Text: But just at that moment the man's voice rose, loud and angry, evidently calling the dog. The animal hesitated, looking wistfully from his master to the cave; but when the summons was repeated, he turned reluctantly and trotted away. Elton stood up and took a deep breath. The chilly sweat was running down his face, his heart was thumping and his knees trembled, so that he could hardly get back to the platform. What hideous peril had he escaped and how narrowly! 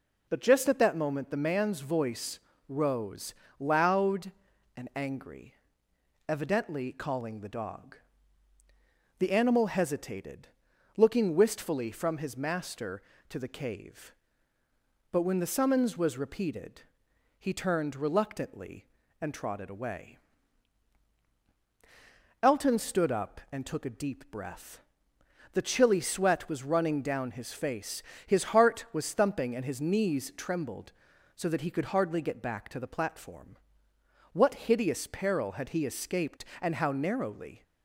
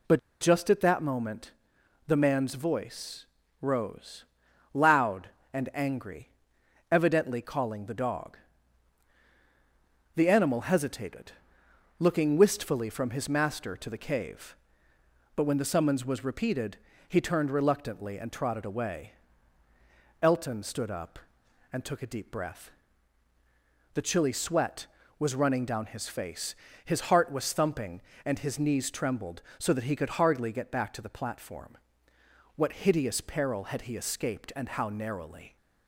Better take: first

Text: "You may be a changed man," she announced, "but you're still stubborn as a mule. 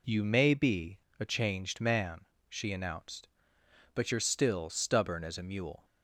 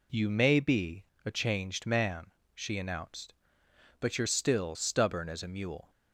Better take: neither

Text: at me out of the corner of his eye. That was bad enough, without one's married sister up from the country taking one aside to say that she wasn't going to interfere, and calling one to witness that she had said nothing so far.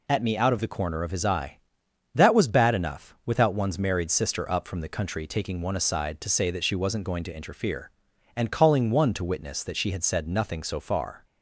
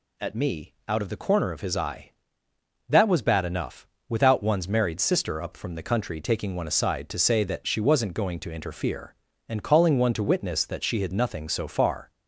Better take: first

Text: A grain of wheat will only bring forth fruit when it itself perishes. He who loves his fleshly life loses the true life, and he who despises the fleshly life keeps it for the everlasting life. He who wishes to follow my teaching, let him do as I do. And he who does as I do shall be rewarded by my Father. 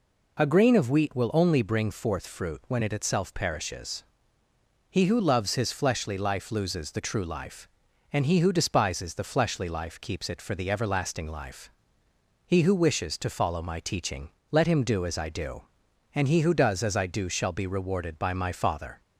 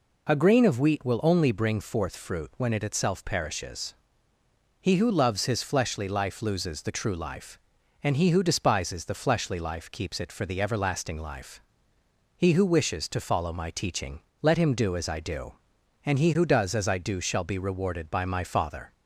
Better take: neither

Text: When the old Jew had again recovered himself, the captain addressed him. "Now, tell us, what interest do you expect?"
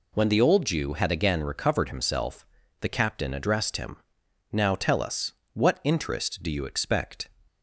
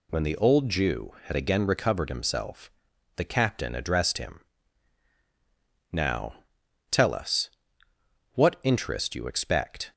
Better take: first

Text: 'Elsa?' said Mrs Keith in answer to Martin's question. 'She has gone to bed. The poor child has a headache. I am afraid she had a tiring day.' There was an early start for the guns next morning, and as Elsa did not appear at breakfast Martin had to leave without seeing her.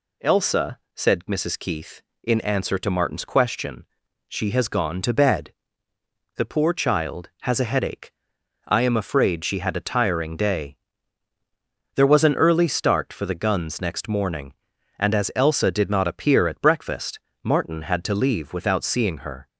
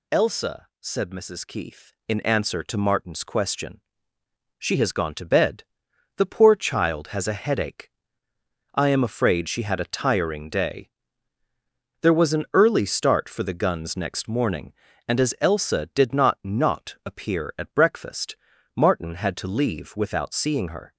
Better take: first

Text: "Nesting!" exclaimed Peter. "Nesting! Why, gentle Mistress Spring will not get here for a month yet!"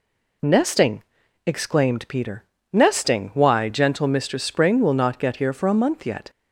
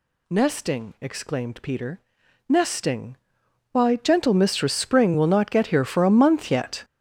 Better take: first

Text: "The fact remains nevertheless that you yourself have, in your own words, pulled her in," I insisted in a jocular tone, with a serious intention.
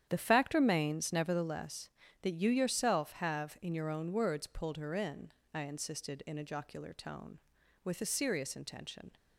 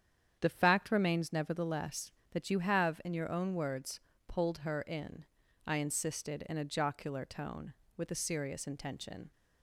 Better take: first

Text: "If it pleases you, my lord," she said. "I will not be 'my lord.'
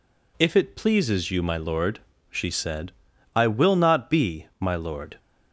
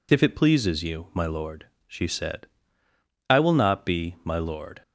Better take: neither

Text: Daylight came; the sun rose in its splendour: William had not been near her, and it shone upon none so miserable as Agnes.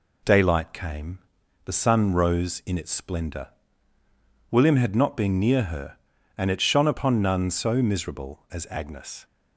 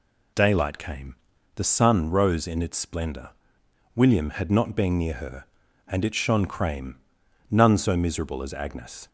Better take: first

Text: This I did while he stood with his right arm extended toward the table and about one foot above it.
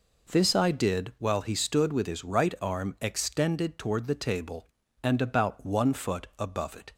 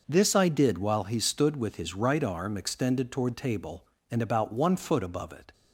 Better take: first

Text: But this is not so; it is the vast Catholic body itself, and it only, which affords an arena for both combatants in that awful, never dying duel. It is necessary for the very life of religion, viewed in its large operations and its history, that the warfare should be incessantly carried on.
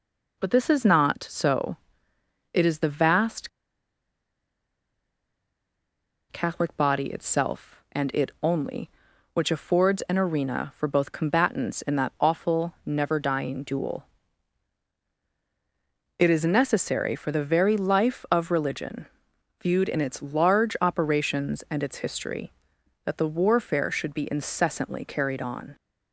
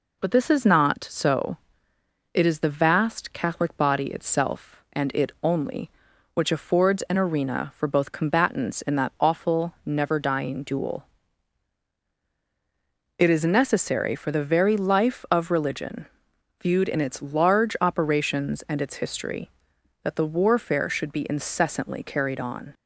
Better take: second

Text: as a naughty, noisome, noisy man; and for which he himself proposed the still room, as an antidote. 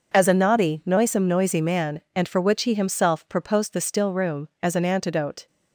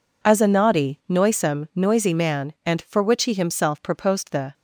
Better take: first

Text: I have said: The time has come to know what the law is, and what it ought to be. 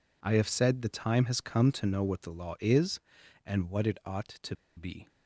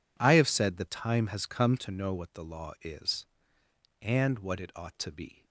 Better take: second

